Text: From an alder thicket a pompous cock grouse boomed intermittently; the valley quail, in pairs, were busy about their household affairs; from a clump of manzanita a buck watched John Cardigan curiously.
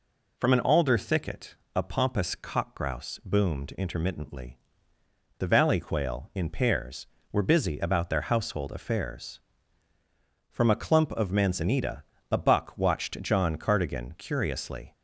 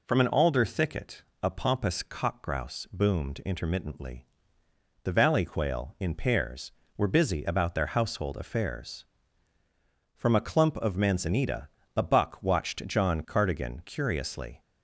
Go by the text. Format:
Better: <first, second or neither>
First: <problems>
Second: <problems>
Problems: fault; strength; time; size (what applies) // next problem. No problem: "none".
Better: neither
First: pauses between "thicket" and "a"; slight; at 1.5 s; 0.20 s long // pauses between "manzanita" and "a"; slight; at 12.0 s; 0.28 s long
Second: pauses between "thicket" and "a"; slight; at 1.2 s; 0.20 s long // pauses between "manzanita" and "a"; slight; at 11.6 s; 0.28 s long